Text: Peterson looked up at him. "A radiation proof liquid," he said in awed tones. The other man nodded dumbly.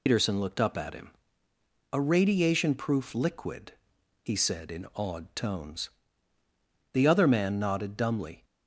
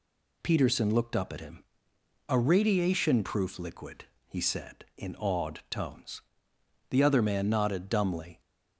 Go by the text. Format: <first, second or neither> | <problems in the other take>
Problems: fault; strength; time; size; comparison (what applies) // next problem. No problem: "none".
second | loses the start of "Peterson"; at 0.0 s; 120 ms